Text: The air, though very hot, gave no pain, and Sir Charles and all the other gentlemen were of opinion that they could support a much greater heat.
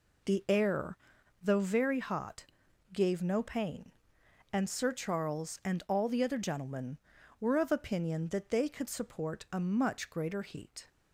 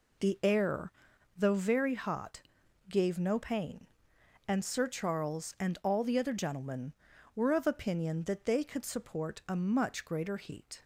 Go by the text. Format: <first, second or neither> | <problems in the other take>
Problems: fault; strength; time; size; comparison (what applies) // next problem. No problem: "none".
neither | none